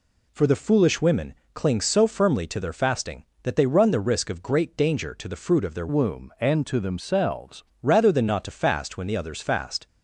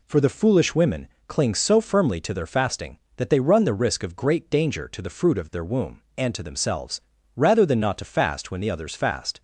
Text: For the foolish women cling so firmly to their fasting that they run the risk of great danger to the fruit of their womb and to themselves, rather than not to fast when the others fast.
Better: second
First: pauses between "women" and "cling"; slight; at 1.3 s; 0.22 s long // changes voice from "womb" to "themselves"; from 5.8 to 7.6 s; 1.8 s long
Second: pauses between "women" and "cling"; slight; at 1.0 s; 0.22 s long

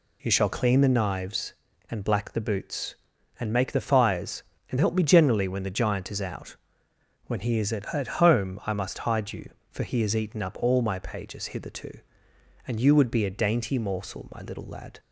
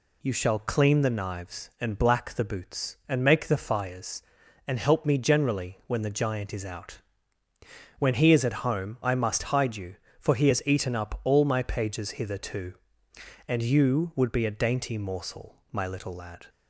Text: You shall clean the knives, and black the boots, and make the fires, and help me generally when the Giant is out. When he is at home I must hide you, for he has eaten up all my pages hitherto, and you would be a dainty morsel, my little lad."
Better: second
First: says "at" twice; at 7.9 s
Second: none

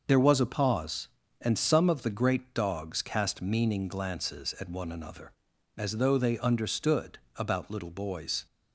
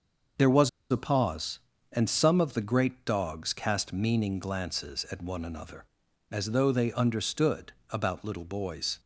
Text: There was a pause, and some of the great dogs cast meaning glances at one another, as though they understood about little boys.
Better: first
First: starts louder than the rest; noticeable; until 1.0 s; 6 dB // pauses between "understood" and "about"; slight; at 7.1 s; 0.16 s long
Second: starts louder than the rest; noticeable; until 1.5 s; 6 dB // pauses between "was" and "a"; slight; at 0.6 s; 0.21 s long // pauses between "understood" and "about"; slight; at 7.7 s; 0.16 s long

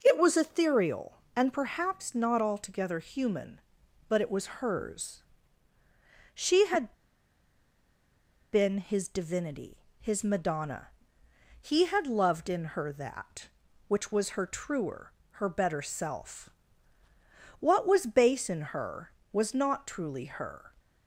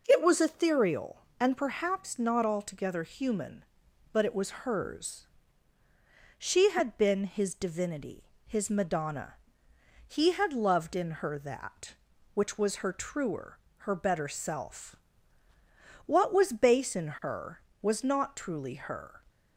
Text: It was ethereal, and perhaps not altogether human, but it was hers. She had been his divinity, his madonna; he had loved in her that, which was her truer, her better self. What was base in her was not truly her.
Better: second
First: pauses between "had" and "been"; strong; at 6.9 s; 1.5 s long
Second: none

